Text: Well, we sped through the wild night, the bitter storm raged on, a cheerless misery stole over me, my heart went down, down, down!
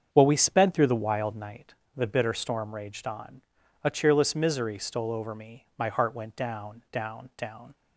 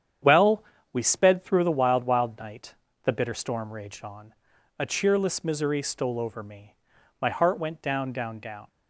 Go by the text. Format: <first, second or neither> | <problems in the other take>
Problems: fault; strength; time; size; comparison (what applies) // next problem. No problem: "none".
first | starts louder than the rest; strong; until 1.5 s; 9 dB; strong in the first // says "wild" twice; at 2.0 s